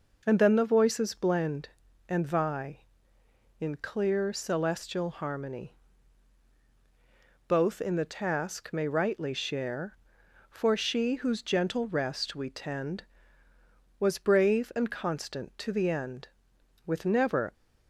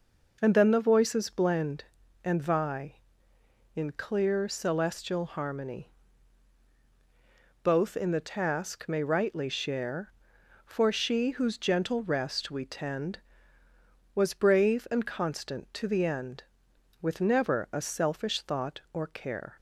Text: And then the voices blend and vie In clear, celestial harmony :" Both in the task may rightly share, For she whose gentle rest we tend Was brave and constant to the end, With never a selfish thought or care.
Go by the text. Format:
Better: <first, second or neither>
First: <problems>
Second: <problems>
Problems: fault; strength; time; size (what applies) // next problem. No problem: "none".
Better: second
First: starts louder than the rest; noticeable; until 1.2 s; 6 dB // stops before "a selfish thought or care"; at 17.5 s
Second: starts louder than the rest; until 1.4 s; 6 dB